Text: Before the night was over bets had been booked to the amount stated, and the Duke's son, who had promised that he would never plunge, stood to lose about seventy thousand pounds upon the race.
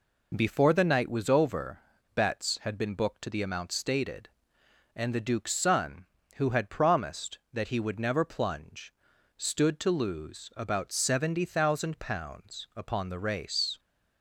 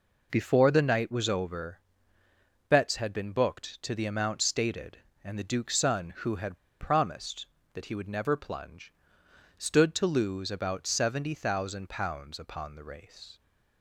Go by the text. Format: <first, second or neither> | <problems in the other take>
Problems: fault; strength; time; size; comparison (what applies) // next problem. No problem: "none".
first | pauses between "over" and "bets"; noticeable; at 1.8 s; 0.88 s long; slight in the first // pauses between "had" and "promised"; slight; at 6.5 s; 0.22 s long